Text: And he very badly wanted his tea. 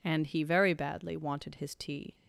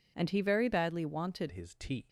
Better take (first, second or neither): first